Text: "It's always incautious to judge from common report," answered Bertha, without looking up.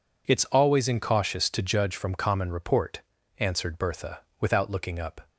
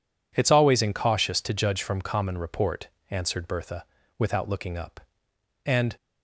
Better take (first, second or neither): first